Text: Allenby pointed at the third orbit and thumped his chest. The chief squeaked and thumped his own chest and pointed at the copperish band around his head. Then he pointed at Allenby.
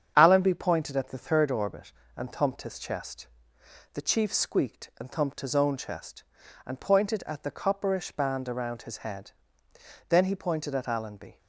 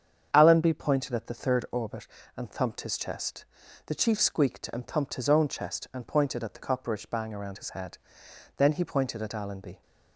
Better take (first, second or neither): first